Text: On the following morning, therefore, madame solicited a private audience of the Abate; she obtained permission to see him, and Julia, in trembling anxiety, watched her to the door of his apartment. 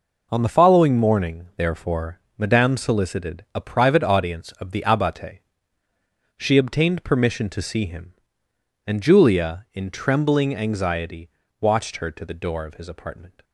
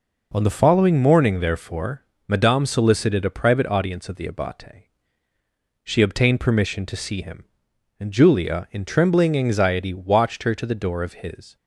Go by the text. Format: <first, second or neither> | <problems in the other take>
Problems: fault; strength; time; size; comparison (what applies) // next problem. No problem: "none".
first | stops before "apartment"; at 11.5 s